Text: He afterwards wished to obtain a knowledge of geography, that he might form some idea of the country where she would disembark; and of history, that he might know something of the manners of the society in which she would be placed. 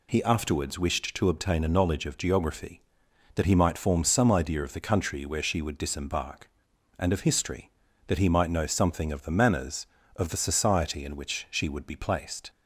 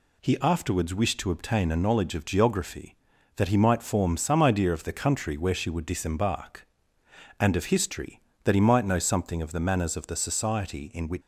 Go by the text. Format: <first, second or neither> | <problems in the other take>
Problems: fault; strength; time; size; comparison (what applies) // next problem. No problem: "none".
first | stops before "she would be placed"; at 11.2 s